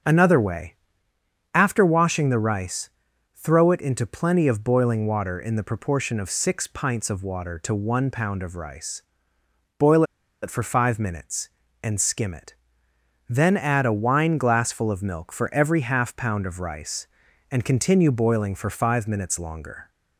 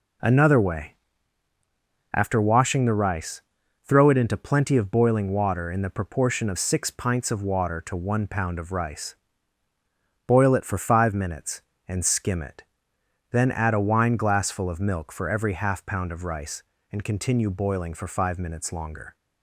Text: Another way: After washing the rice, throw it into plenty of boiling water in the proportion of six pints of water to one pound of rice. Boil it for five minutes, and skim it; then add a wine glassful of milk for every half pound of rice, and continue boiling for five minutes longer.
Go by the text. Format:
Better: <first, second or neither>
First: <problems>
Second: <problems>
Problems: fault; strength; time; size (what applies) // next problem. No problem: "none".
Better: second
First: starts louder than the rest; until 1.8 s; 7 dB // pauses between "Boil" and "it"; at 10.0 s; 0.39 s long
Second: none